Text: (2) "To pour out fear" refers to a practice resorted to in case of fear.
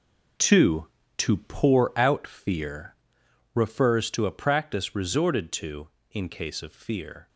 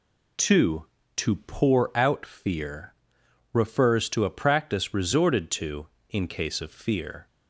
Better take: second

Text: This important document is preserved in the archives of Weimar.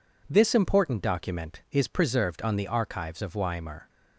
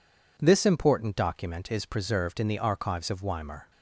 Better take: second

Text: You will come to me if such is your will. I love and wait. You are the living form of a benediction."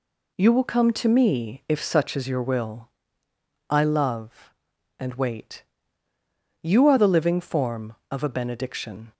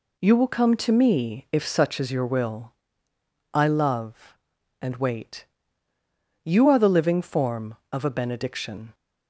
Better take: neither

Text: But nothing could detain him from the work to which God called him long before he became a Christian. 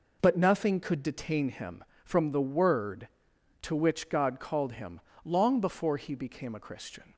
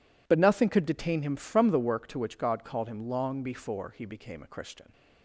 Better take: second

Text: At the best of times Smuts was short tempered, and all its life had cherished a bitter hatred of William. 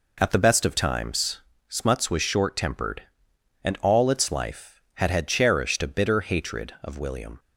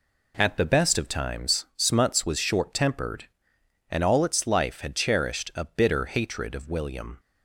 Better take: second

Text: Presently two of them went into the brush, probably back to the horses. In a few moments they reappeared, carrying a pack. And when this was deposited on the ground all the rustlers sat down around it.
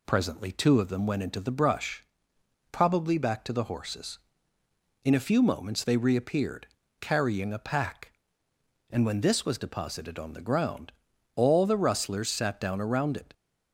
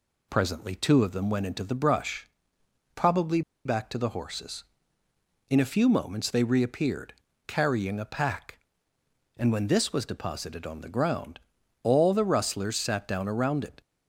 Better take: first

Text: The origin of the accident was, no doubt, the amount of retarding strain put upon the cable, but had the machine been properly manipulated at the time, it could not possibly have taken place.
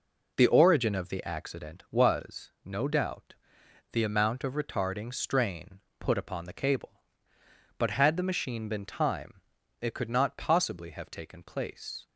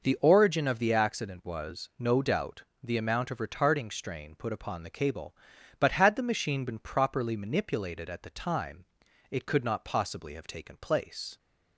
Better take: second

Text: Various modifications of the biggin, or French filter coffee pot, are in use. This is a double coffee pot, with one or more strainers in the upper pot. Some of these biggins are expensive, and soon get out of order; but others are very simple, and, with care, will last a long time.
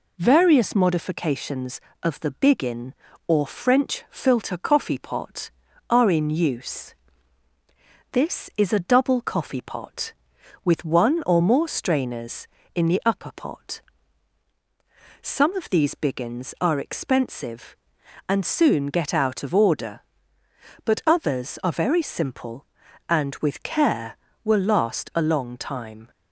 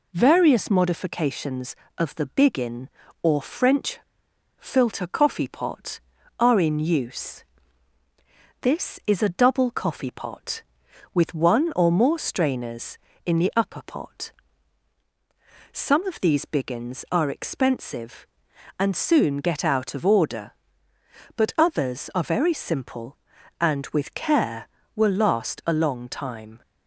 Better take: first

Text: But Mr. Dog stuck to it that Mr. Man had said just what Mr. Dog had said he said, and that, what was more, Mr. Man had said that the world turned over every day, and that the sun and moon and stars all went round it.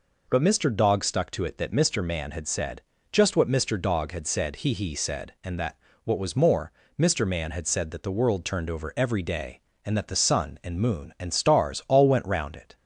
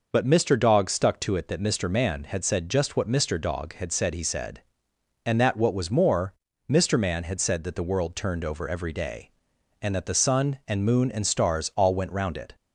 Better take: second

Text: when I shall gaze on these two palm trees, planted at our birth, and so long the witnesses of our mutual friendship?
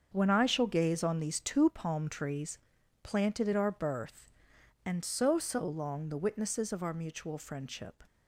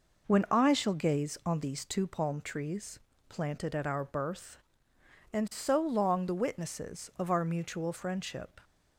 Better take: second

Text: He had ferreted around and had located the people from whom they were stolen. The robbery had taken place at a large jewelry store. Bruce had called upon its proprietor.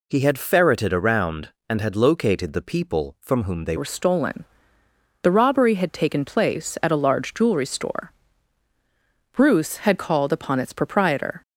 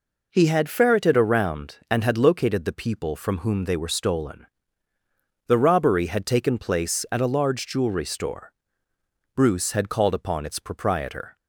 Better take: second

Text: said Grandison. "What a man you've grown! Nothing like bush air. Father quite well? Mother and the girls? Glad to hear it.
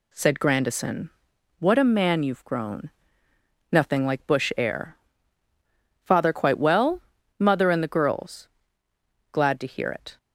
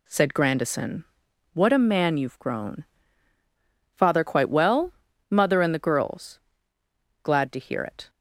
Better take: first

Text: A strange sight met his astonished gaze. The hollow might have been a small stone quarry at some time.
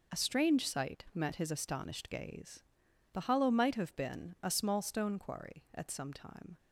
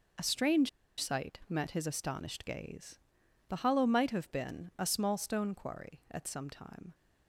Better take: first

